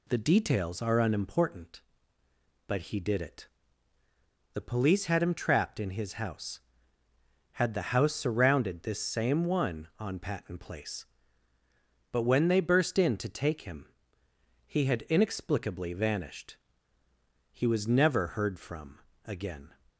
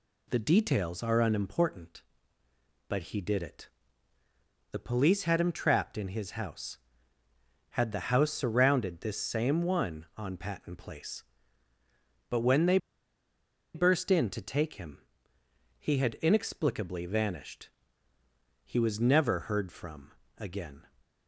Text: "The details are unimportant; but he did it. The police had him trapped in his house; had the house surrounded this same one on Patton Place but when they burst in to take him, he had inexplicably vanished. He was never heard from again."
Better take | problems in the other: first | pauses between "they" and "burst"; noticeable; at 12.7 s; 0.97 s long // pauses between "from" and "again"; slight; at 20.1 s; 0.24 s long; slight in the first

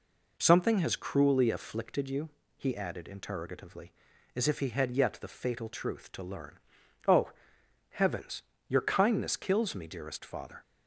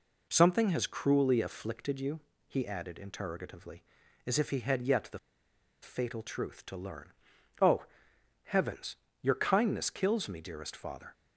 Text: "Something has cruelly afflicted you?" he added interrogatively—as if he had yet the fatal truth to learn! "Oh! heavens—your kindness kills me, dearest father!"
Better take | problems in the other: first | pauses between "the" and "fatal"; noticeable; at 5.1 s; 0.63 s long

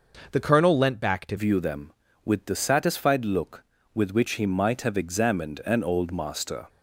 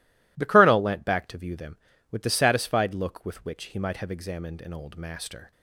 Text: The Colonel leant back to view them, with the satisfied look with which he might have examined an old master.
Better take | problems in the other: second | changes voice at "view"; from 1.3 s on; 5.3 s long

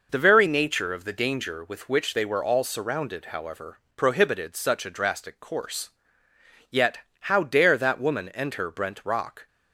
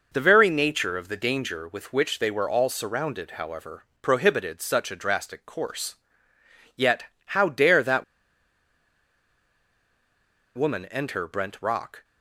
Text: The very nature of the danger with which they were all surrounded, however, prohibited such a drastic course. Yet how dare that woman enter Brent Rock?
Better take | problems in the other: first | pauses between "Yet" and "how"; slight; at 7.0 s; 0.22 s long; slight in the first // pauses between "that" and "woman"; strong; at 8.0 s; 2.5 s long

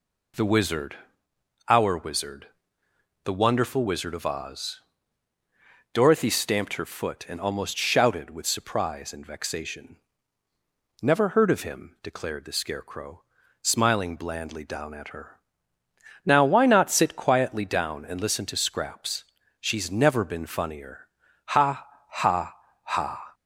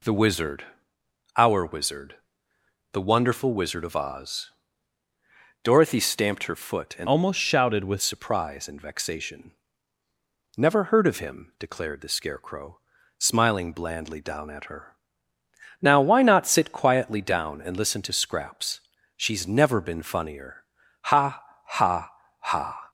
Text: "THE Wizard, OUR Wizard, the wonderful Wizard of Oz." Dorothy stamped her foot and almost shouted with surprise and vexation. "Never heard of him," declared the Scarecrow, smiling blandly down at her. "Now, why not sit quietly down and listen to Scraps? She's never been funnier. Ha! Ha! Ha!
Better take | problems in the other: first | changes voice from "almost" to "with"; from 7.0 to 8.0 s; 1.0 s long

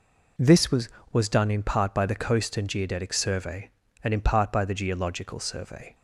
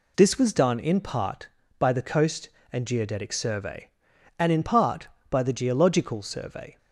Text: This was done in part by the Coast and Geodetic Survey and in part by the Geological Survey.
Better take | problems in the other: second | says "was" twice; at 1.1 s

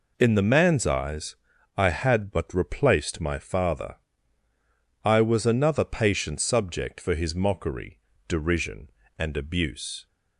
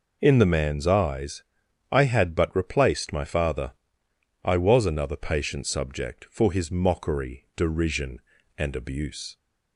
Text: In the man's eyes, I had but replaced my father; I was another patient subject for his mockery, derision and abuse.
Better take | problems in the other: neither | none

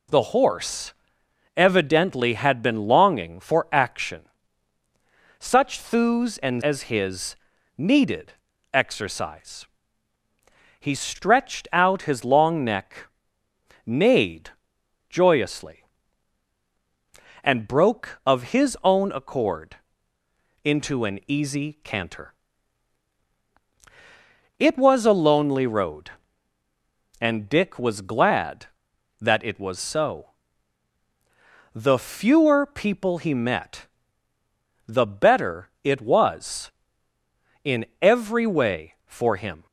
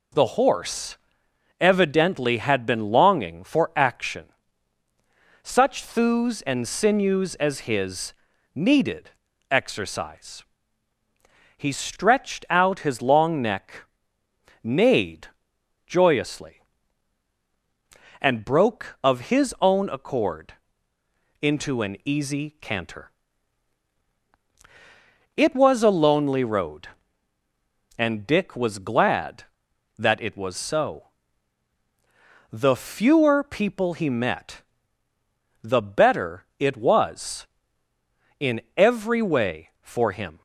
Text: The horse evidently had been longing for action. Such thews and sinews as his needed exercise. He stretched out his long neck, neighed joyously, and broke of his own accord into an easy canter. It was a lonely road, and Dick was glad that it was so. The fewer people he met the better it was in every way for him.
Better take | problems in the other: second | pauses between "horse" and "evidently"; noticeable; at 0.9 s; 0.62 s long; noticeable in the second // skips "sinews"; at 6.6 s // pauses between "his" and "needed"; at 7.3 s; 0.40 s long; also in the second // pauses between "needed" and "exercise"; at 8.3 s; 0.40 s long; also in the second // pauses between "neighed" and "joyously"; noticeable; at 14.4 s; 0.60 s long; noticeable in the second // pauses between "accord" and "into"; noticeable; at 19.7 s; 0.88 s long; noticeable in the second // pauses between "met" and "the"; at 33.8 s; 1.0 s long; also in the second // pauses between "in" and "every"; slight; at 37.8 s; 0.16 s long; slight in the second

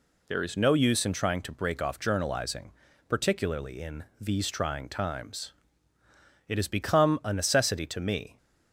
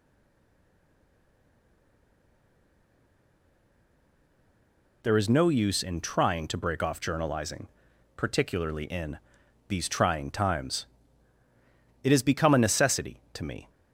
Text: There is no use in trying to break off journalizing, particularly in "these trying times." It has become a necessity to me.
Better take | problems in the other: first | stays silent before the first word; strong; until 5.0 s; 5.0 s long // pauses between "in" and "these"; noticeable; at 9.1 s; 0.52 s long

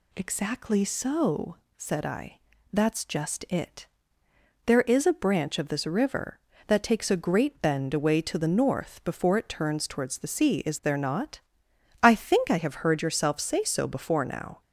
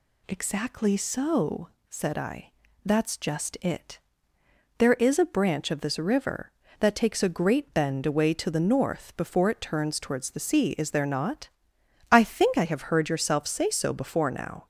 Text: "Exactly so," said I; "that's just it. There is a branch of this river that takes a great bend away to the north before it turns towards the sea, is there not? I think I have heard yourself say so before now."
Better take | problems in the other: neither | none

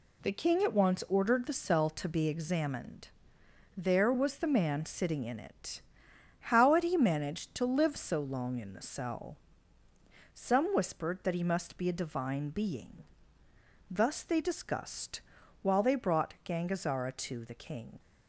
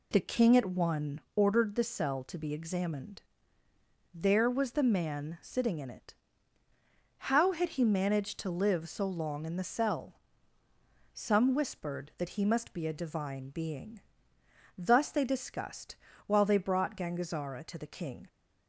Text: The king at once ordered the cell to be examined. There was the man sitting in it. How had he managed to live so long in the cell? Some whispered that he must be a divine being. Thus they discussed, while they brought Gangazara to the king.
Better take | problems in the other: first | says "one" for "once"; at 0.6 s

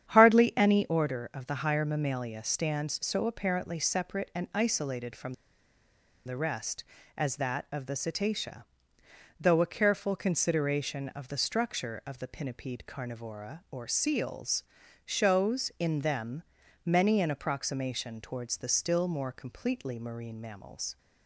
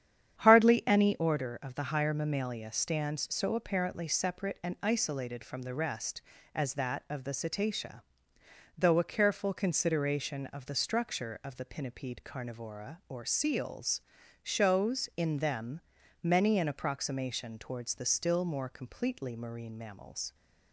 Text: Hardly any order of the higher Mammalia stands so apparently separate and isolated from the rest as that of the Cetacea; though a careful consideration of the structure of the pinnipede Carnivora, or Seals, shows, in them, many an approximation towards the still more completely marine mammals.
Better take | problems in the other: second | starts louder than the rest; strong; until 1.1 s; 9.5 dB; strong in the second // pauses between "from" and "the"; noticeable; at 5.3 s; 0.93 s long

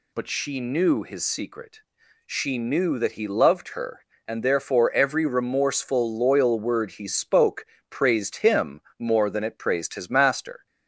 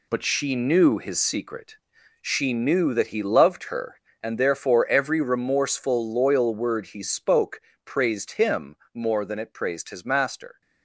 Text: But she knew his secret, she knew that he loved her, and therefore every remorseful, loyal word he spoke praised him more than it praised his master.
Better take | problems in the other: first | gets quieter; strong; throughout; 9 dB // pauses between "spoke" and "praised"; slight; at 7.6 s; 0.24 s long; slight in the first // pauses between "him" and "more"; slight; at 8.7 s; 0.20 s long; slight in the first

